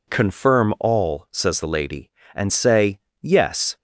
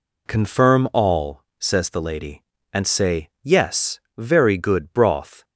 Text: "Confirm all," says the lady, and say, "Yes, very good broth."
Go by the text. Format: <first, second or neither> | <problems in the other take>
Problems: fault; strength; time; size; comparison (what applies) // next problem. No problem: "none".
second | stops before "very good broth"; at 3.7 s